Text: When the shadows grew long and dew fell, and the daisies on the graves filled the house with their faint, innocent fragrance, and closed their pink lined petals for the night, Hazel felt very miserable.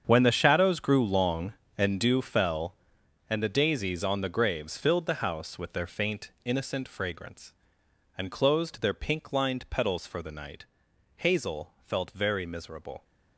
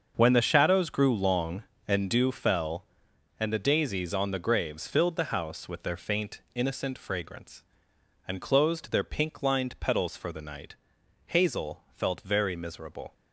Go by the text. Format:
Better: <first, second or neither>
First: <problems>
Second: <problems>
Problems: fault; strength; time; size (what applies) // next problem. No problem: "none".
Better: second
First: gets quieter; strong; throughout; 13.5 dB // starts louder than the rest; strong; until 1.0 s; 7.5 dB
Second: starts louder than the rest; until 1.1 s; 6.5 dB